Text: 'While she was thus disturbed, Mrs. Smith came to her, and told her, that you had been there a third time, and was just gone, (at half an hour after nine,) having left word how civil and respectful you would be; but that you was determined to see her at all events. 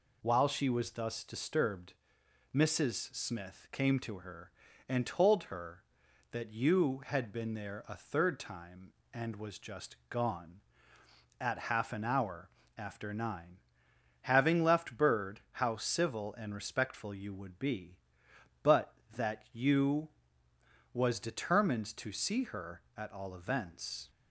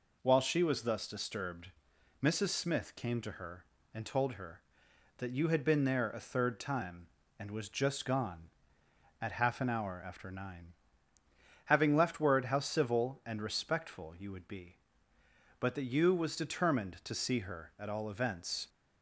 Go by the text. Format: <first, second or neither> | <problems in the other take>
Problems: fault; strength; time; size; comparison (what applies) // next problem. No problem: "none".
second | pauses between "hour" and "after"; slight; at 12.4 s; 0.28 s long // says "bird" for "word"; at 14.9 s